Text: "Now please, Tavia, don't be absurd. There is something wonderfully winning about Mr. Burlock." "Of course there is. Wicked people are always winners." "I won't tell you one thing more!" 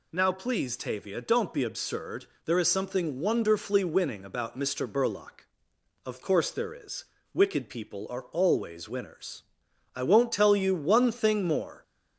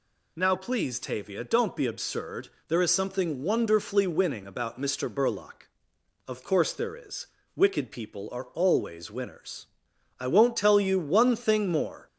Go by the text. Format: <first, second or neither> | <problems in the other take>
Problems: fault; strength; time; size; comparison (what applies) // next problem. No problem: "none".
neither | none